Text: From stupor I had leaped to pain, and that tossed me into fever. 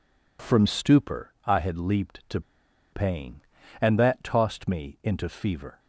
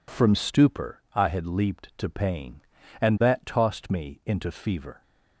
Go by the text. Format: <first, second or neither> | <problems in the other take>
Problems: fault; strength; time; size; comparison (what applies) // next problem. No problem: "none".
second | pauses between "to" and "pain"; noticeable; at 2.4 s; 0.51 s long